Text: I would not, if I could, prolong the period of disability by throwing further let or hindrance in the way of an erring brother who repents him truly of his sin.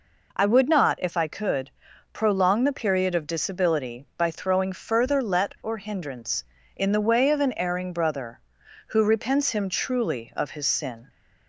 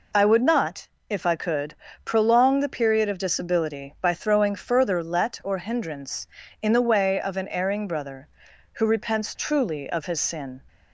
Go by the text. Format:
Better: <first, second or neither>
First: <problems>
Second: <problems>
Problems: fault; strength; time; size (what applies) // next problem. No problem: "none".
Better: first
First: none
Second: skips "him"; at 9.3 s